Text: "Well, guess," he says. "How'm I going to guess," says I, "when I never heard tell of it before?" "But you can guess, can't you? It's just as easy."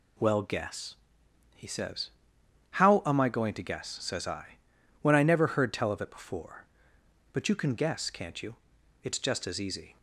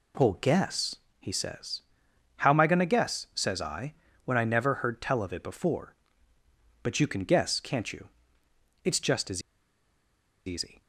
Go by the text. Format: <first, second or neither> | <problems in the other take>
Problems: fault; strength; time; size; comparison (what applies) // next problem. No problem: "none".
first | pauses between "as" and "easy"; at 9.4 s; 1.0 s long